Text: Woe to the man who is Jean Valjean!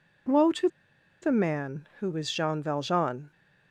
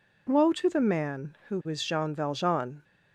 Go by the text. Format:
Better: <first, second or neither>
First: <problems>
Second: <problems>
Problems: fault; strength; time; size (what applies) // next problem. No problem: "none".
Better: second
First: pauses between "to" and "the"; noticeable; at 0.6 s; 0.54 s long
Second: none